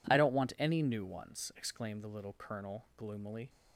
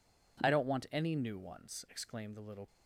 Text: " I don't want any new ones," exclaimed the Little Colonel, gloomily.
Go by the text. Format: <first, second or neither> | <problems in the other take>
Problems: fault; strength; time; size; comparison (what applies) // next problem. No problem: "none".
first | stops before "Colonel gloomily"; at 2.6 s